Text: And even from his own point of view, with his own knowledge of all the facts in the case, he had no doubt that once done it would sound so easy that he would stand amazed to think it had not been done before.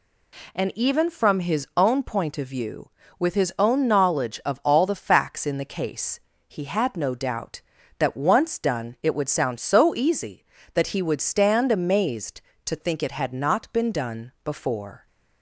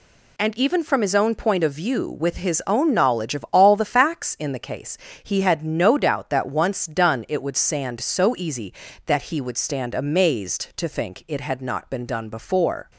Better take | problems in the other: first | says "sand" for "sound"; at 7.5 s

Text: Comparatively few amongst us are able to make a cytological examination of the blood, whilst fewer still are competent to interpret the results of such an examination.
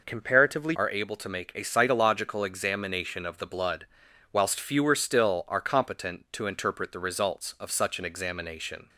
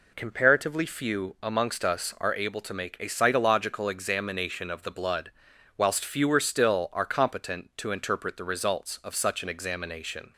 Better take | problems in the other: second | skips "few amongst us"; at 0.7 s

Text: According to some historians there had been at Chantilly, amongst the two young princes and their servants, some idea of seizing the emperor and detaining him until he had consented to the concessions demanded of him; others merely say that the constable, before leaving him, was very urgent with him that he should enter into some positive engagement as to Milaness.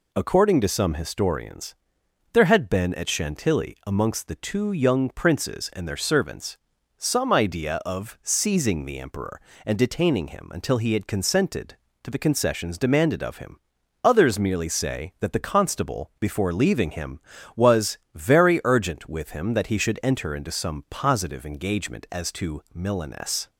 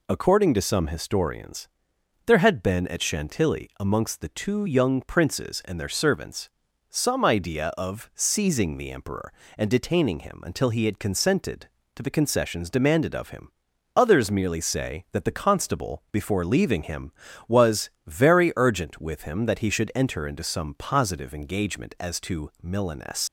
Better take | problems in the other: first | pauses between "historians" and "there"; noticeable; at 1.6 s; 0.60 s long; noticeable in the first // pauses between "was" and "very"; slight; at 17.8 s; 0.16 s long; slight in the first // leaves "Milaness" unfinished; at 23.2 s; 100 ms

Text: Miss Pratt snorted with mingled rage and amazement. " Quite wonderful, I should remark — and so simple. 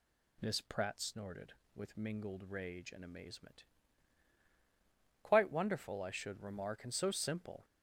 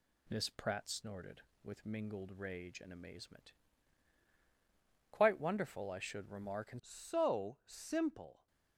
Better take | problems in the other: first | changes voice at "so"; from 6.8 s on; 1.6 s long

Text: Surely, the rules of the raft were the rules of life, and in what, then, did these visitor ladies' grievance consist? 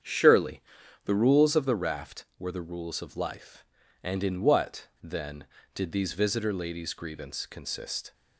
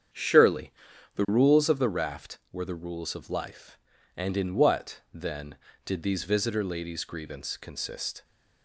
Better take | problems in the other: neither | starts louder than the rest; strong; the same in both

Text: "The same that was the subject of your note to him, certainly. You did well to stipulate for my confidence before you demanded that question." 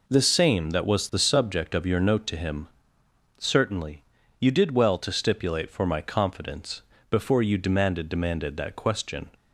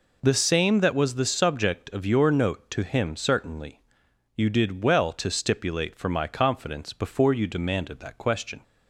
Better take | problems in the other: second | pauses between "confidence" and "before"; slight; at 6.7 s; 0.30 s long // says "demanded" twice; at 8.0 s

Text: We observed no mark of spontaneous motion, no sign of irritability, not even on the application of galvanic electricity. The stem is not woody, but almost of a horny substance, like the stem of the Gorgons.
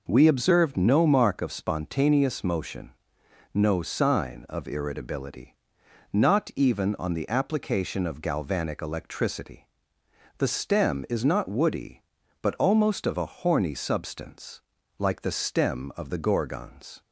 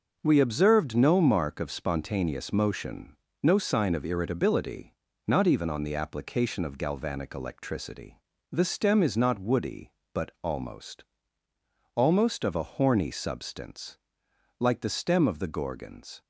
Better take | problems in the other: first | says "almost" twice; at 11.9 s

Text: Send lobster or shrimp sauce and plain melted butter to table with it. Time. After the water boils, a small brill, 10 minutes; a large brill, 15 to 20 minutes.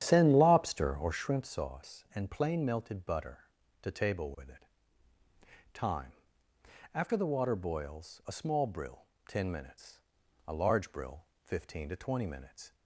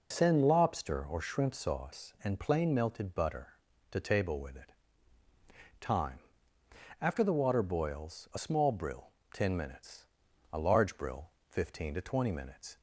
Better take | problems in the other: second | starts louder than the rest; strong; until 1.4 s; 10 dB

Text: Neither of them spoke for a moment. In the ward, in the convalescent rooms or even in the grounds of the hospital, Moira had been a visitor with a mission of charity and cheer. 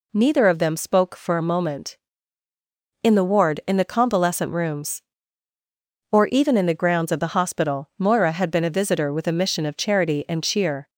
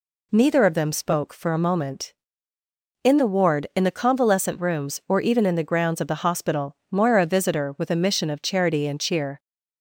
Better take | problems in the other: first | skips "had been"; at 7.2 s

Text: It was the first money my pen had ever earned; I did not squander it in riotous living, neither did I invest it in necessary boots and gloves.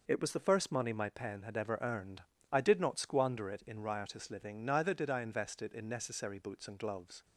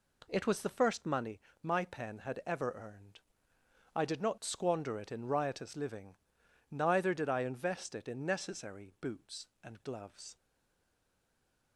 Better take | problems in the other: first | pauses between "money" and "my"; slight; at 1.4 s; 0.22 s long // stays silent after the last word; noticeable; from 10.3 s on; 1.4 s long

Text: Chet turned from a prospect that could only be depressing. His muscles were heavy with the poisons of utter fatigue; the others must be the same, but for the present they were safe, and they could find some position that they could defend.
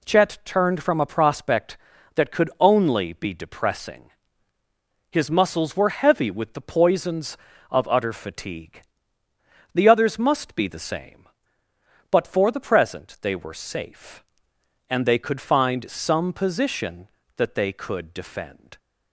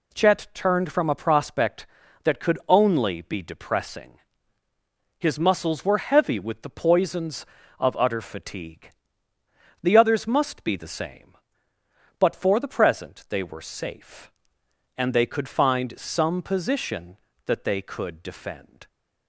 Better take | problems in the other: neither | none

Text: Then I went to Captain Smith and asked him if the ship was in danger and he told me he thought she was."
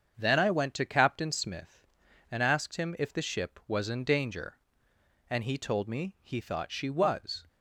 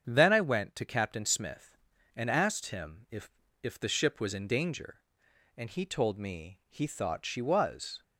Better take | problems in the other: first | starts louder than the rest; strong; until 1.0 s; 7.5 dB; strong in the first // says "if" twice; at 3.6 s

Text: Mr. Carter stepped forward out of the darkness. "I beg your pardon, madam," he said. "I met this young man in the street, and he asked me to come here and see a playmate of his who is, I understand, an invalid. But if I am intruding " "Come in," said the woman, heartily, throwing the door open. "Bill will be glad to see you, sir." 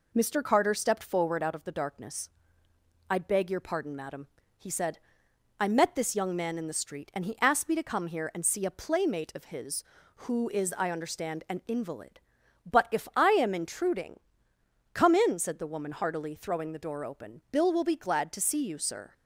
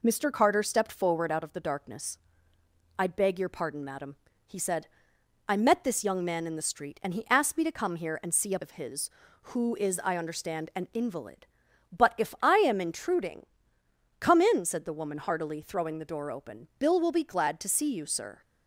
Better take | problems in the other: first | skips "playmate"; at 8.5 s

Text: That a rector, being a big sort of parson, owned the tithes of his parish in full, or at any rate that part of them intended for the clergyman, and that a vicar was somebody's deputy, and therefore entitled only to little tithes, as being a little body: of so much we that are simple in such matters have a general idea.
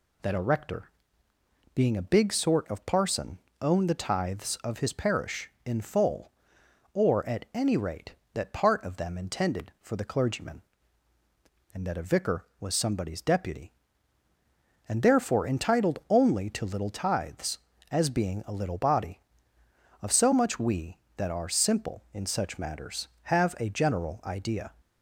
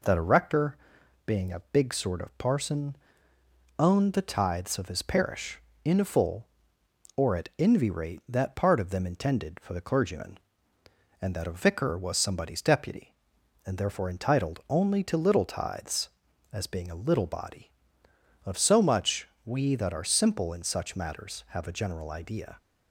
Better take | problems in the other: first | says "envy" for "any"; at 7.5 s // pauses between "much" and "we"; slight; at 19.2 s; 0.16 s long

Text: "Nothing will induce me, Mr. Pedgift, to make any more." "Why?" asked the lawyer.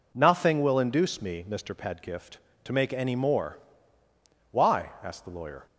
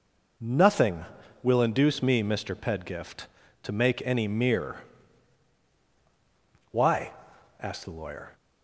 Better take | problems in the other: first | says "mere" for "more"; at 4.2 s

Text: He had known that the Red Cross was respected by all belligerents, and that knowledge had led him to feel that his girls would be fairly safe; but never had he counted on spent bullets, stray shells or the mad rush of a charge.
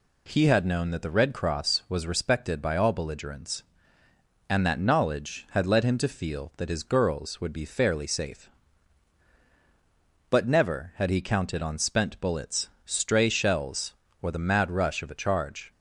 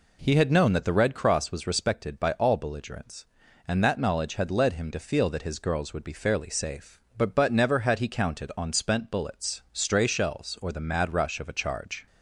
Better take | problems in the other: first | says "but" twice; at 7.3 s

